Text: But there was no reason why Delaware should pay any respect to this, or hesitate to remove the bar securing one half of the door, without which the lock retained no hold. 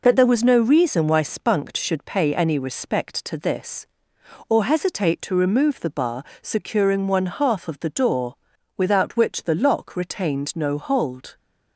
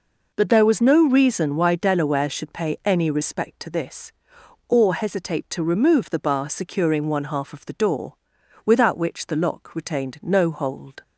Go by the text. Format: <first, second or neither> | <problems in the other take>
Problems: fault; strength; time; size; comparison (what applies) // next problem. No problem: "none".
second | says "Spunked" for "Delaware"; at 1.2 s // pauses between "bar" and "securing"; slight; at 6.2 s; 0.20 s long